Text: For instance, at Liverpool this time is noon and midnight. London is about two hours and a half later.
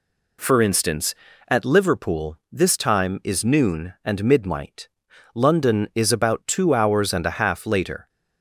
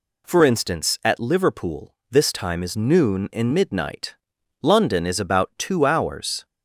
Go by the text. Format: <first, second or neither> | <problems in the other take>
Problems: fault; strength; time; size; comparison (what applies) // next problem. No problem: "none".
first | pauses between "Liverpool" and "this"; slight; at 1.9 s; 0.18 s long // stops before "and a half later"; at 6.4 s